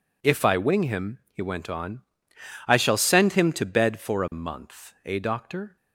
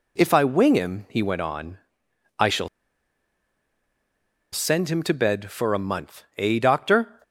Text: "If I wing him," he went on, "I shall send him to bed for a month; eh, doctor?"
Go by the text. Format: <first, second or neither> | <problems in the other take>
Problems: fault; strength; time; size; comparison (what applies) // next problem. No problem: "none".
first | pauses between "shall" and "send"; strong; at 2.6 s; 1.8 s long